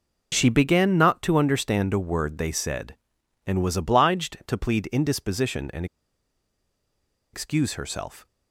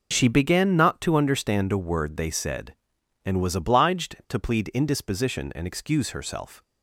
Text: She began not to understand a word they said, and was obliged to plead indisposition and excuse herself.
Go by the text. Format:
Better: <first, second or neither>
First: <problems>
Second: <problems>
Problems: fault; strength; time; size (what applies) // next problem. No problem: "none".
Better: second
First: pauses between "and" and "excuse"; strong; at 5.8 s; 1.4 s long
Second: none